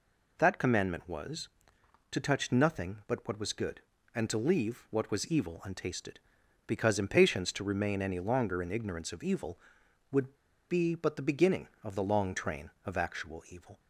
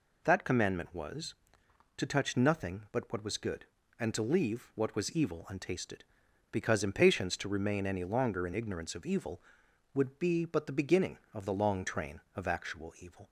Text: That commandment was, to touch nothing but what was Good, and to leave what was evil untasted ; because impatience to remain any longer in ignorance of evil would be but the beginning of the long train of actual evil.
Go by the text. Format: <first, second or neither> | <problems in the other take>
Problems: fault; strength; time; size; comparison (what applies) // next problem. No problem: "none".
second | pauses between "would" and "be"; slight; at 10.3 s; 0.33 s long